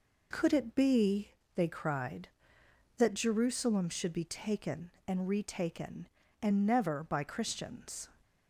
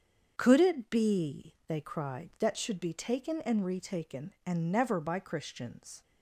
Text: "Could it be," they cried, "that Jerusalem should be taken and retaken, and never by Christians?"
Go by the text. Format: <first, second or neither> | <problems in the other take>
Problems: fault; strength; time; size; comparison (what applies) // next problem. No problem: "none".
first | starts louder than the rest; strong; until 1.3 s; 7 dB // skips "Jerusalem"; at 2.5 s